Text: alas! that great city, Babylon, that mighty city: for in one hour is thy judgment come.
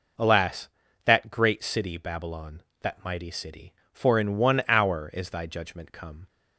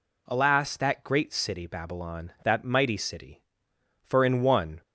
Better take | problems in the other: first | stops before "hour is thy judgment come"; at 4.8 s

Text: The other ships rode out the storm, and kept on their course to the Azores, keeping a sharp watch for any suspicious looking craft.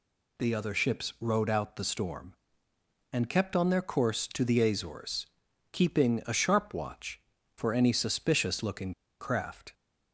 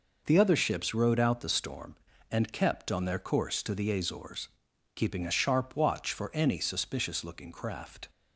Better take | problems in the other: second | pauses between "looking" and "craft"; slight; at 8.9 s; 0.29 s long

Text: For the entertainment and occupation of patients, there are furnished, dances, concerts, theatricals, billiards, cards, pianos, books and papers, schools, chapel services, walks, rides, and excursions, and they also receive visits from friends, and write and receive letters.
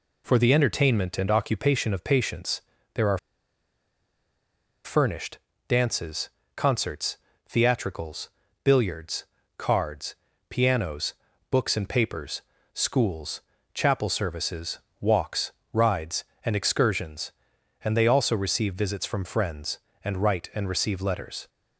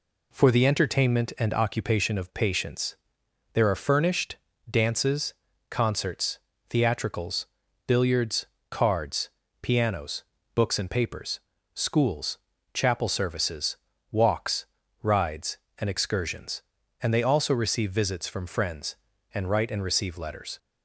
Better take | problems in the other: second | pauses between "are" and "furnished"; strong; at 3.1 s; 1.6 s long

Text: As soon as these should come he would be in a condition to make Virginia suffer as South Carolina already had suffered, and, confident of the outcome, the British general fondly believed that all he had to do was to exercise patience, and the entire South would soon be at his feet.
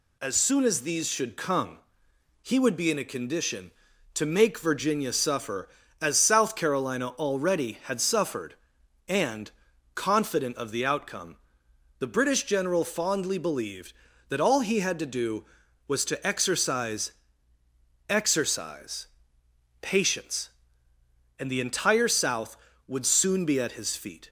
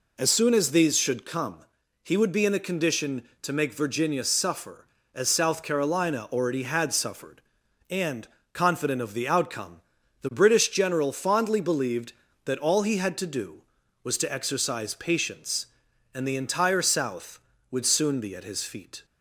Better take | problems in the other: second | pauses between "come" and "he"; noticeable; at 1.7 s; 0.64 s long; noticeable in the second // says "exercise" twice; at 18.0 s

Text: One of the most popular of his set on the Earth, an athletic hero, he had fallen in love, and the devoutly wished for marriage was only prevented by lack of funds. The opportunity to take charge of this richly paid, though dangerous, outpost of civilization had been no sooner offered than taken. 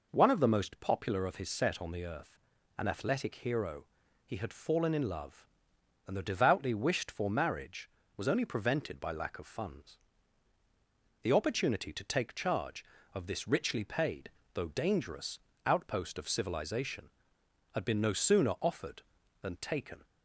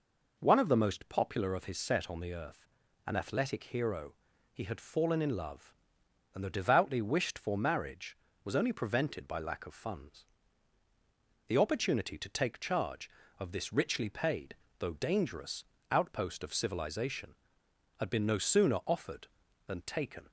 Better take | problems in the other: neither | none

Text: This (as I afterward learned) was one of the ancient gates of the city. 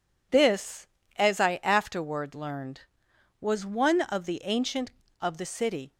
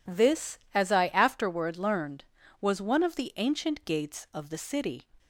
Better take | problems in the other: second | skips "gates"; at 5.1 s

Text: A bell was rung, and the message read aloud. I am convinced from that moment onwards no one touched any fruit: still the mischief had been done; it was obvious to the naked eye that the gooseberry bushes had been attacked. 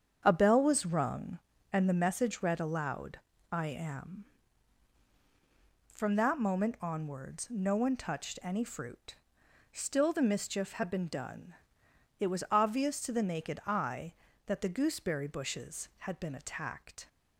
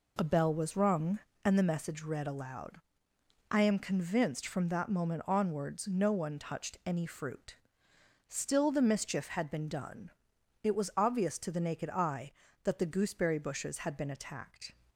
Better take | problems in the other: second | starts louder than the rest; strong; until 1.2 s; 7.5 dB // skips "convinced"; at 5.0 s

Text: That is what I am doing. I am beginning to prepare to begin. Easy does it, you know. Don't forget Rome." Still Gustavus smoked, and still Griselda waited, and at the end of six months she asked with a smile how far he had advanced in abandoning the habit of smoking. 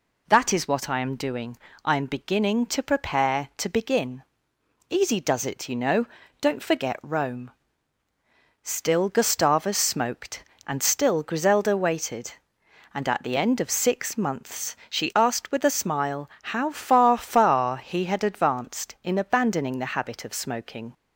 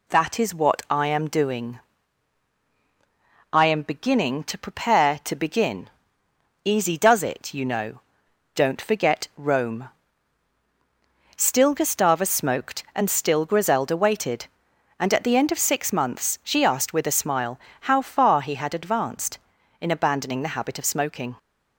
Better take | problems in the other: second | pauses between "smile" and "how"; slight; at 16.2 s; 0.24 s long; slight in the second // says "far" twice; at 17.1 s

